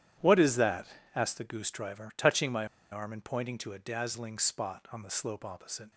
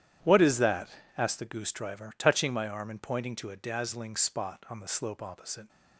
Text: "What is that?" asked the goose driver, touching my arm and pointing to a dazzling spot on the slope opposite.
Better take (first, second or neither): second